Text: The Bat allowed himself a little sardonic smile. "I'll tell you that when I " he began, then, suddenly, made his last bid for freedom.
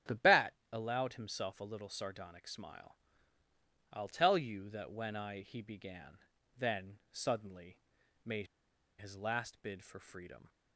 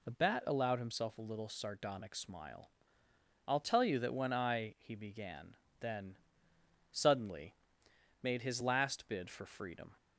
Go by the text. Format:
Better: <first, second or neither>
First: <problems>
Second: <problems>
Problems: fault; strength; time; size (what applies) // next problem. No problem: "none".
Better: second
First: starts louder than the rest; strong; until 1.2 s; 9 dB // pauses between "Bat" and "allowed"; slight; at 0.5 s; 0.18 s long // pauses between "made" and "his"; noticeable; at 8.4 s; 0.51 s long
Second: none